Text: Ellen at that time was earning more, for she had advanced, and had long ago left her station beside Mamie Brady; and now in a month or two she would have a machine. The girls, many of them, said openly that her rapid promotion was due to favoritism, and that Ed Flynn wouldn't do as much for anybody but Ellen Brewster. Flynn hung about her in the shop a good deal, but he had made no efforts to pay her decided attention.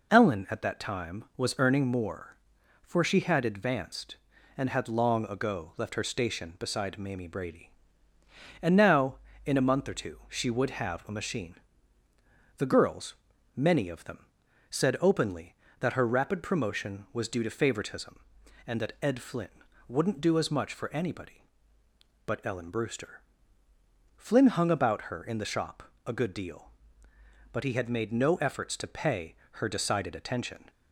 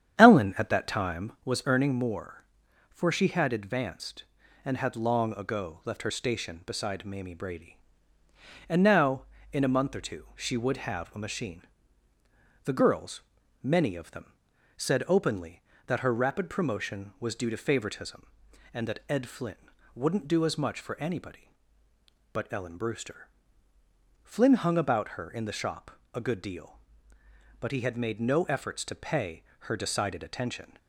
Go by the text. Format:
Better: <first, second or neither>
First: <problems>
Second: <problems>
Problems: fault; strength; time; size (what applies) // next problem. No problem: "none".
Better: first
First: pauses between "Flynn" and "wouldn't"; at 19.4 s; 0.40 s long // pauses between "shop" and "a"; slight; at 25.8 s; 0.22 s long // pauses between "pay" and "her"; slight; at 29.3 s; 0.24 s long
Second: starts louder than the rest; strong; until 1.5 s; 9 dB // pauses between "Flynn" and "wouldn't"; at 19.5 s; 0.40 s long // pauses between "shop" and "a"; slight; at 25.9 s; 0.22 s long // pauses between "pay" and "her"; slight; at 29.4 s; 0.24 s long